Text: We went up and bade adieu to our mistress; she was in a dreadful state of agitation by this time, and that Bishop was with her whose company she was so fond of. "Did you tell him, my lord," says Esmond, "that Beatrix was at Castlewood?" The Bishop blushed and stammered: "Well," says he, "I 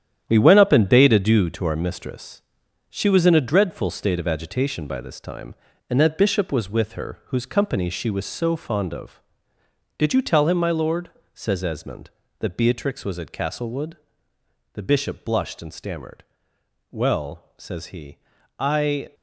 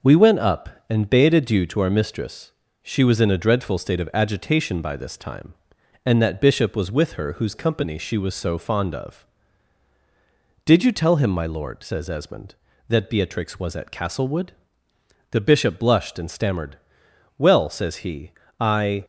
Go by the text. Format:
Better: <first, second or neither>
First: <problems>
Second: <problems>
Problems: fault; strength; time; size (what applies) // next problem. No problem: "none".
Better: second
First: gets quieter; strong; throughout; 9 dB // starts louder than the rest; strong; until 1.2 s; 10 dB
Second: starts louder than the rest; until 1.2 s; 6.5 dB